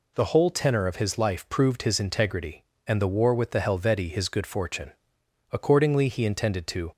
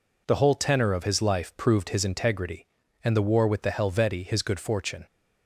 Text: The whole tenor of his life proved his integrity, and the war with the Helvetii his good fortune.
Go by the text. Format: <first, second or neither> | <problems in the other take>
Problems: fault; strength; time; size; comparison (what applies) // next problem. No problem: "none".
second | goes on to say "Accordingly he intended to"; from 5.5 s on; 1.4 s long